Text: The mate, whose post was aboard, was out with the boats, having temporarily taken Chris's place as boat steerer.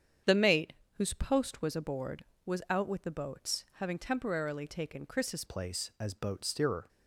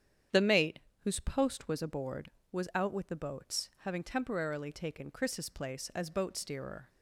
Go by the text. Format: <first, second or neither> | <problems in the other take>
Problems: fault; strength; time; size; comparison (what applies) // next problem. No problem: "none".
second | starts louder than the rest; strong; until 1.5 s; 8 dB; strong in the second // changes voice at "place"; from 5.4 s on; 1.4 s long